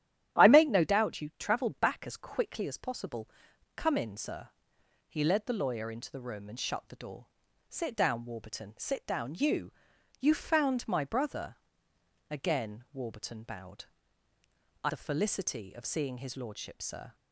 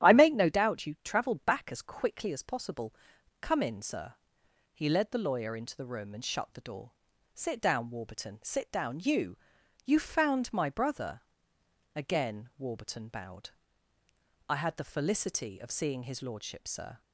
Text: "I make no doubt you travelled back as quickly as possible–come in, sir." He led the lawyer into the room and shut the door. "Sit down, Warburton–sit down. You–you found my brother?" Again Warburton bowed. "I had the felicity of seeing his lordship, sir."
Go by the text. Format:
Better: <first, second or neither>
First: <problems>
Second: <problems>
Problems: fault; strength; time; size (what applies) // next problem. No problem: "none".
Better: second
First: starts louder than the rest; strong; until 1.4 s; 11.5 dB // skips "had"; at 14.8 s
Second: starts louder than the rest; strong; until 1.1 s; 11.5 dB